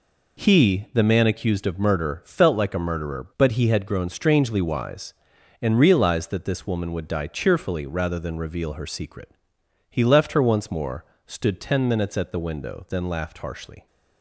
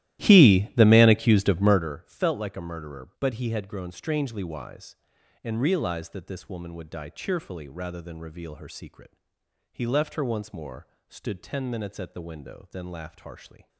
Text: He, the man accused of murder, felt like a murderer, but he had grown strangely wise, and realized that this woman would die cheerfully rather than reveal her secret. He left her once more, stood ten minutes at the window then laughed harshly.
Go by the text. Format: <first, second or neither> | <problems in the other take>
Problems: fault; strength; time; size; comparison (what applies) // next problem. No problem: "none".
first | starts louder than the rest; strong; until 2.0 s; 14.5 dB